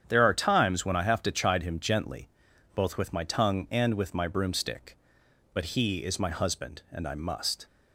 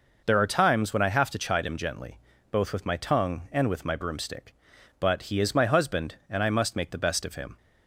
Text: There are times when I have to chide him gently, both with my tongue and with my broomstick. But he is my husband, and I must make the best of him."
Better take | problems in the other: second | starts louder than the rest; strong; until 1.0 s; 8.5 dB // stops before "make the best of him"; at 7.6 s

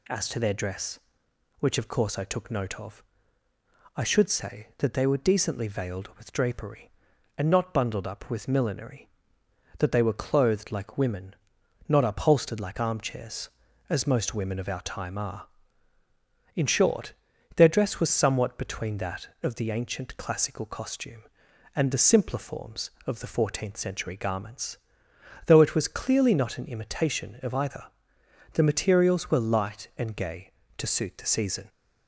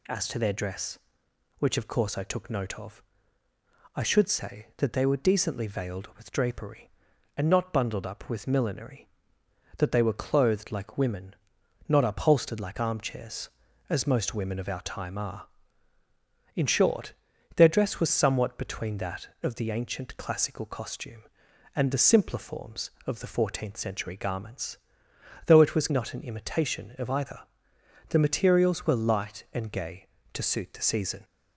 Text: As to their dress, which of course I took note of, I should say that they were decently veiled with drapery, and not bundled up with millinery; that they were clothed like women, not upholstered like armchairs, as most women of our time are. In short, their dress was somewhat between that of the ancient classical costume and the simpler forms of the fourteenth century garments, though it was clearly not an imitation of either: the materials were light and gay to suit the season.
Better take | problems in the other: first | skips "clearly"; at 25.8 s

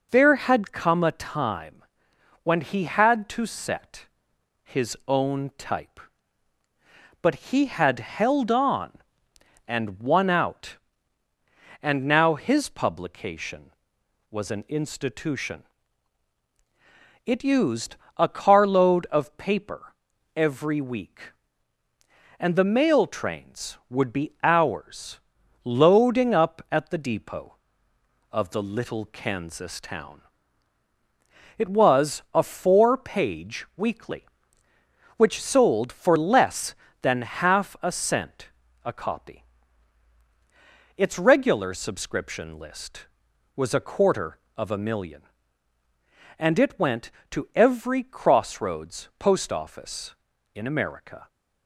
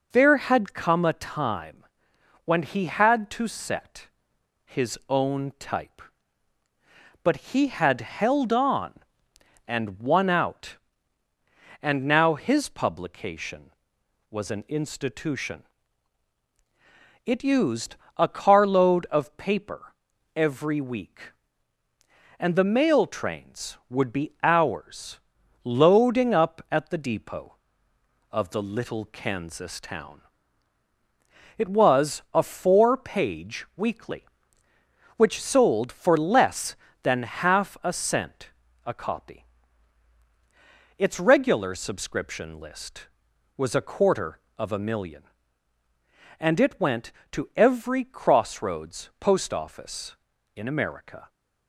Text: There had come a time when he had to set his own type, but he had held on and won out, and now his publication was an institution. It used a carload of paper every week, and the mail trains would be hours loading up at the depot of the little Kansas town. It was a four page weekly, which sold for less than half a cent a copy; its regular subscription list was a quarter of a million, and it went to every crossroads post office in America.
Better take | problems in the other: neither | pauses between "time" and "when"; noticeable; the same in both // pauses between "set" and "his"; noticeable; the same in both // pauses between "but" and "he"; slight; the same in both // pauses between "used" and "a"; slight; the same in both // pauses between "paper" and "every"; the same in both // pauses between "hours" and "loading"; the same in both // pauses between "cent" and "a"; slight; the same in both

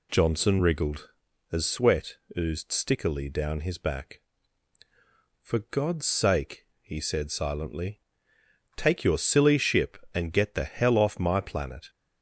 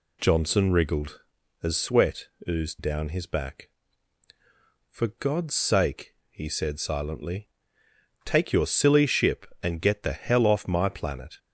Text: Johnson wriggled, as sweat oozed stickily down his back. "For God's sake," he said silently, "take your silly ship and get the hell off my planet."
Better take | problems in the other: first | pauses between "sweat" and "oozed"; slight; at 2.2 s; 0.24 s long; slight in the first // skips "stickily"; at 2.7 s

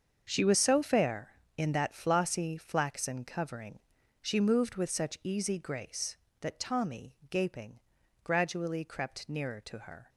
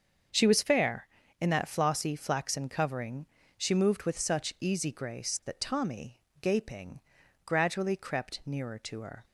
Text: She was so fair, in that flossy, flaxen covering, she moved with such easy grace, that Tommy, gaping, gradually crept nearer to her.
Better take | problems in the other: first | starts louder than the rest; until 1.6 s; 7 dB; also in the first // skips "so"; at 0.6 s

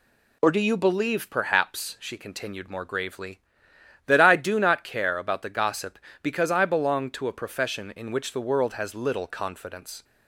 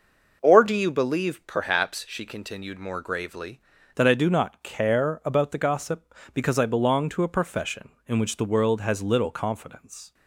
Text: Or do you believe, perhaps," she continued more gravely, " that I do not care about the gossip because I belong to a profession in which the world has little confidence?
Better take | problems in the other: first | changes voice at "that"; from 3.9 s on; 6.2 s long

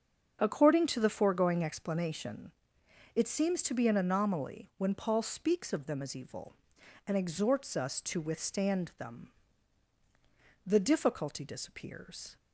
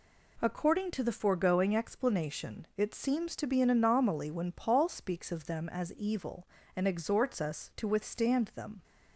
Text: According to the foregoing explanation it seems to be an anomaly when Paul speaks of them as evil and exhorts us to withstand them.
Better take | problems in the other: second | starts louder than the rest; strong; until 1.4 s; 7.5 dB // pauses between "explanation" and "it"; noticeable; at 2.5 s; 0.62 s long // goes on to say "The difficulty disappears"; strong; from 10.6 s on; 1.7 s long

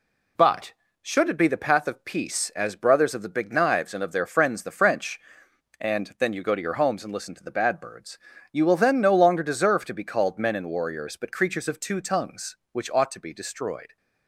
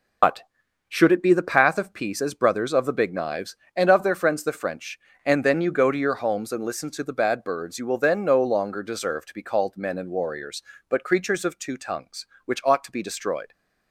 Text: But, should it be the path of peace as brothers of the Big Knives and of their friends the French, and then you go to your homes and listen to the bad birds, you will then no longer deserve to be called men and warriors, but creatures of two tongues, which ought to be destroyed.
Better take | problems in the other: first | loses the start of "But"; at 0.2 s; 80 ms

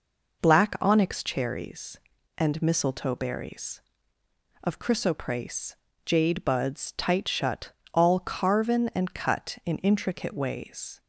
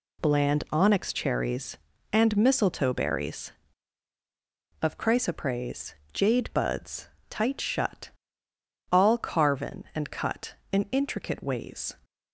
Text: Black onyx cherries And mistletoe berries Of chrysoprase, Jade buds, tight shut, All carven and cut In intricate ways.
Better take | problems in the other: first | says "Bland" for "Black"; at 0.2 s

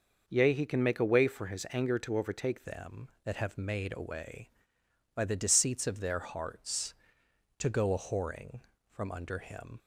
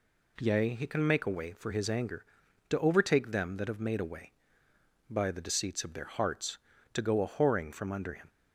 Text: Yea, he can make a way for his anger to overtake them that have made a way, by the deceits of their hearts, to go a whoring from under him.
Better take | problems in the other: second | changes voice at "them"; from 2.6 s on; 7.1 s long

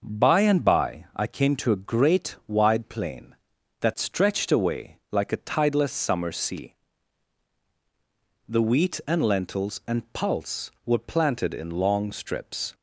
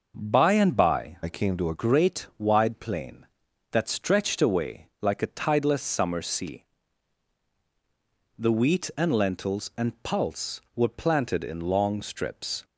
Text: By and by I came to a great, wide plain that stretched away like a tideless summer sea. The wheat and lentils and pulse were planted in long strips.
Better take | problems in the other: first | changes voice from "I" to "a"; from 1.2 to 1.7 s; 0.5 s long

